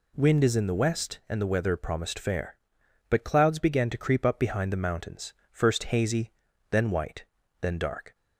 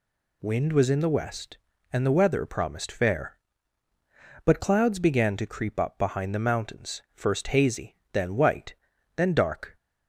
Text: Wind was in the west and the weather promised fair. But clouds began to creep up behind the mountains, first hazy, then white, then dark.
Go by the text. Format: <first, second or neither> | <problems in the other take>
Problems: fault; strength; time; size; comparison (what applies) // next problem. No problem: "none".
second | says "is" for "was"; at 0.4 s